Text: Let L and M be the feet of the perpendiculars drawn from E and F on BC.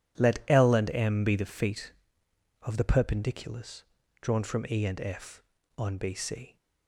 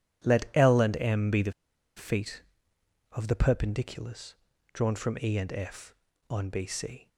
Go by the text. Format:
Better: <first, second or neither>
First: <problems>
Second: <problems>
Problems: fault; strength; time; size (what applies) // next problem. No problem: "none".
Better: first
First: pauses between "perpendiculars" and "drawn"; at 3.8 s; 0.37 s long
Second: pauses between "the" and "feet"; at 1.5 s; 0.45 s long // pauses between "perpendiculars" and "drawn"; at 4.3 s; 0.38 s long